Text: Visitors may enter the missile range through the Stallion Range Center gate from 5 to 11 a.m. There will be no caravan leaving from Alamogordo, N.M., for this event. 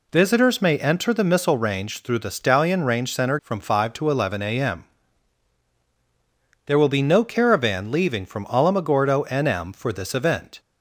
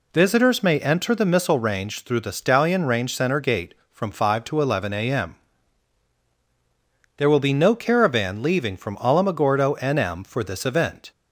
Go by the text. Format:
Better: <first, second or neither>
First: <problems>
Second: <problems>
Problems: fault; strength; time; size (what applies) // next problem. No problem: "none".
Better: second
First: skips "gate"; at 3.3 s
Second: none